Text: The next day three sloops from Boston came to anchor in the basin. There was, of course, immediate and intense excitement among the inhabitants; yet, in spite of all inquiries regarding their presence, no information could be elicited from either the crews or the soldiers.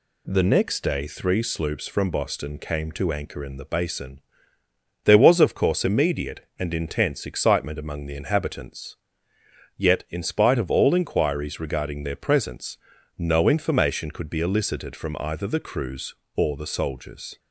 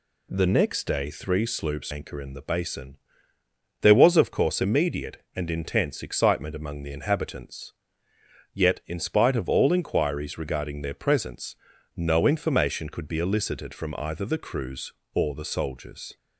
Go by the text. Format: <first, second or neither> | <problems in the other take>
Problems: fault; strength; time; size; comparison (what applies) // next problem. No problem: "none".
first | skips "from Boston came to"; at 1.9 s